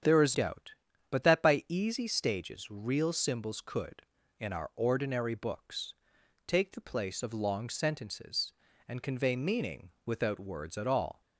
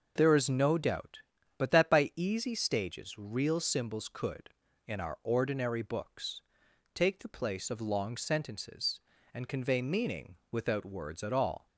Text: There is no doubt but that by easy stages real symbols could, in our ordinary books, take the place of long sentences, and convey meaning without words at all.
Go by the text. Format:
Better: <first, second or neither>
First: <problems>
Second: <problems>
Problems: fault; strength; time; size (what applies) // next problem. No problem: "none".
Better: second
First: starts louder than the rest; strong; until 1.4 s; 8 dB // skips "no"; at 0.3 s // pauses between "meaning" and "without"; slight; at 9.9 s; 0.16 s long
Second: pauses between "meaning" and "without"; slight; at 10.3 s; 0.16 s long